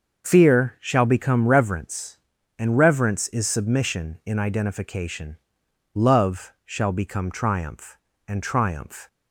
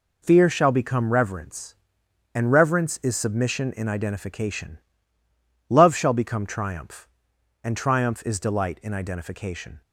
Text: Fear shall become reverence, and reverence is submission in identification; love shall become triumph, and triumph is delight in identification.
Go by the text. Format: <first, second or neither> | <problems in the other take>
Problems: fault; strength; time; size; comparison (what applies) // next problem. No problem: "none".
second | starts louder than the rest; until 1.3 s; 6 dB // stops before "is delight in identification"; at 9.0 s